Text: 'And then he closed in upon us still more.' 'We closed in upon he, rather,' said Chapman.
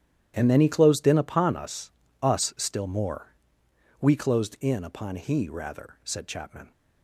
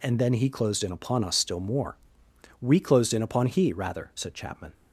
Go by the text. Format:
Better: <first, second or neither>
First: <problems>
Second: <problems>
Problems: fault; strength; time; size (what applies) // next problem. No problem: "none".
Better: second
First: starts louder than the rest; strong; until 1.3 s; 11.5 dB // says "us" twice; at 2.2 s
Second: none